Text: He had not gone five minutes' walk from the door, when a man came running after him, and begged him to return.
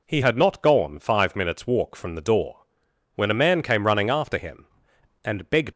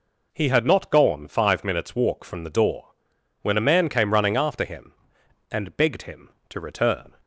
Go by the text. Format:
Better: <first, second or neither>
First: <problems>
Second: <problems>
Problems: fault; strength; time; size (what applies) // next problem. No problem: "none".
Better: second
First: stops before "him to return"; at 5.7 s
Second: none